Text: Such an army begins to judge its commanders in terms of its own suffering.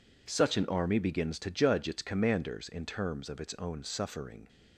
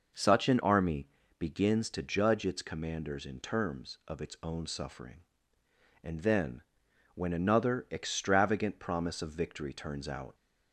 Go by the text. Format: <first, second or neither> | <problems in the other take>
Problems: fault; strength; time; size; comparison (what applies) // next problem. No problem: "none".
first | pauses between "army" and "begins"; slight; at 1.0 s; 0.32 s long // goes on to say "And then when another extravagant promise of victory turns out"; strong; from 6.0 s on; 4.3 s long